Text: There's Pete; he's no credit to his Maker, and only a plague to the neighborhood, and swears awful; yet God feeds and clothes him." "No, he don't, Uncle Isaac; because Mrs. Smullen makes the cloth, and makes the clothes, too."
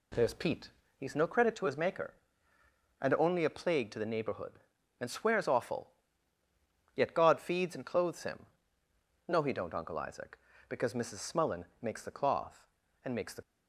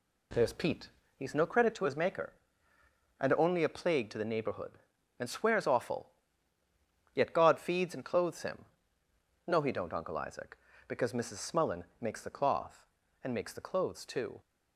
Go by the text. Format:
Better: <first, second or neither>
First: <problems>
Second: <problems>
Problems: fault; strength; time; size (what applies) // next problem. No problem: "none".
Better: second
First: pauses between "Smullen" and "makes"; slight; at 11.6 s; 0.16 s long // stops before "clothes too"; at 13.4 s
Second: pauses between "Smullen" and "makes"; slight; at 11.8 s; 0.16 s long